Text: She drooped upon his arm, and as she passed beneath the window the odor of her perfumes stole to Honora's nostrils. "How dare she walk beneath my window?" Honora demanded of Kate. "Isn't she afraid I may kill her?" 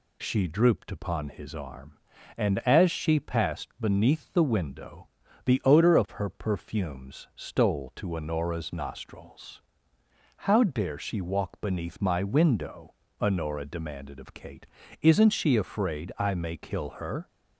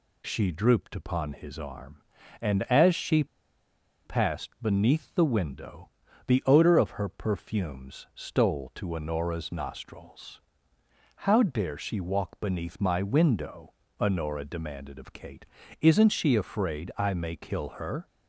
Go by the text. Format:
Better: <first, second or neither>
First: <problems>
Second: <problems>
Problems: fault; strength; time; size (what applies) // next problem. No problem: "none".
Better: first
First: pauses between "window" and "the"; at 5.0 s; 0.38 s long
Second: pauses between "she" and "passed"; noticeable; at 3.2 s; 0.80 s long // pauses between "window" and "the"; at 5.8 s; 0.38 s long